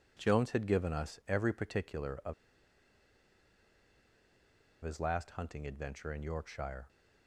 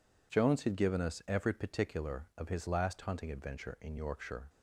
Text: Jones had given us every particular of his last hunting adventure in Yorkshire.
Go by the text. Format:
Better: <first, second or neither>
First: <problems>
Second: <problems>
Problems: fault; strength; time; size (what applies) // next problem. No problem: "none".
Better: second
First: pauses between "of" and "his"; strong; at 2.3 s; 2.4 s long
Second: none